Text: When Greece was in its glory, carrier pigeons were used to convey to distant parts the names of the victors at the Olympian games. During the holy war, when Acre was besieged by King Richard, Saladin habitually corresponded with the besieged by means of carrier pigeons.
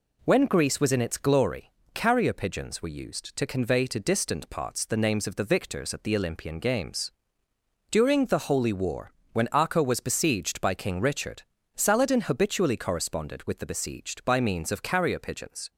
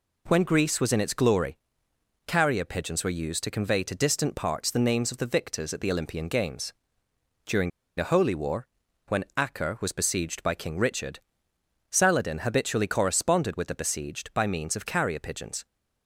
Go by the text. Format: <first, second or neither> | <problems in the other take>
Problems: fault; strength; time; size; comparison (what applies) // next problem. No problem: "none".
first | pauses between "During" and "the"; slight; at 7.6 s; 0.28 s long